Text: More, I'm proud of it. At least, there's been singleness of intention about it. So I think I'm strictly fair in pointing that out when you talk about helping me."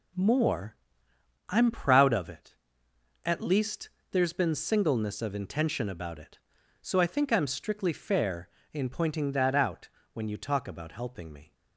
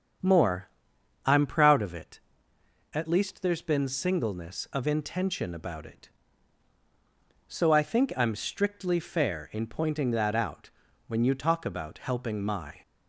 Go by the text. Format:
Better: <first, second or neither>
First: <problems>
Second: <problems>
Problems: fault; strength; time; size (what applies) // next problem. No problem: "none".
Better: first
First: pauses between "out" and "when"; slight; at 9.8 s; 0.24 s long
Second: starts louder than the rest; strong; until 1.7 s; 7.5 dB // pauses between "out" and "when"; at 10.6 s; 0.38 s long // says "my" for "me"; at 12.4 s